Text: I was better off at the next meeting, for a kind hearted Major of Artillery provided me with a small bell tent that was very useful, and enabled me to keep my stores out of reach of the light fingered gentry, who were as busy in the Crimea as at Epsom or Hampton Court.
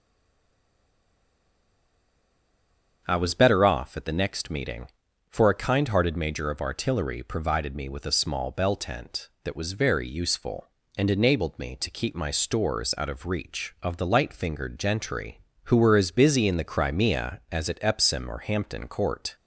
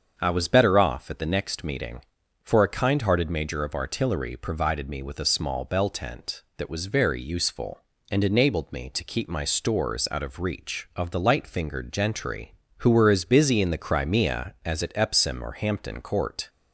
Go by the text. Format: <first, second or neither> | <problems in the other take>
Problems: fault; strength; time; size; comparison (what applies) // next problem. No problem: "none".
second | stays silent before the first word; strong; until 3.0 s; 3.0 s long // starts louder than the rest; until 4.0 s; 7 dB; also in the second